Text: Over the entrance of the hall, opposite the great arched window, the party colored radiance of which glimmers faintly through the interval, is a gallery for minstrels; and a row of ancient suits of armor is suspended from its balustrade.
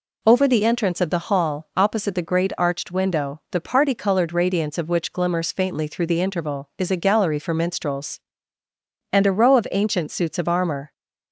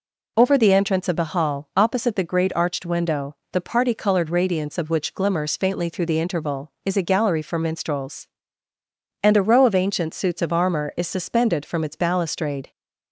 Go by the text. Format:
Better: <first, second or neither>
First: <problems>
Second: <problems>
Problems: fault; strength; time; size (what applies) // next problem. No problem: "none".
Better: second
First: stops before "is suspended from its balustrade"; at 10.9 s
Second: none